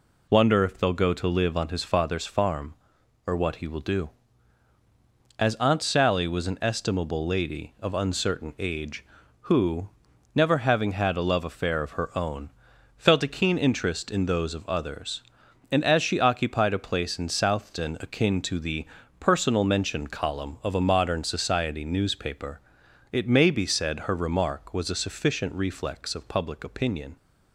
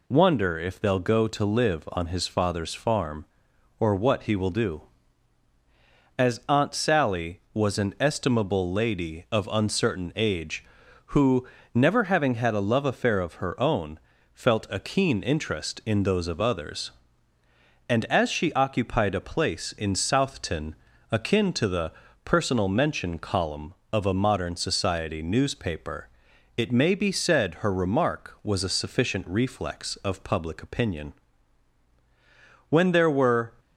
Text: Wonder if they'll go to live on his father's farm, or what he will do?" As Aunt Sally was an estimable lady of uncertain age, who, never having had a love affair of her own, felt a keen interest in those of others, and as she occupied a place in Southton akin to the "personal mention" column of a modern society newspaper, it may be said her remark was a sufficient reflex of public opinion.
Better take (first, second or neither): first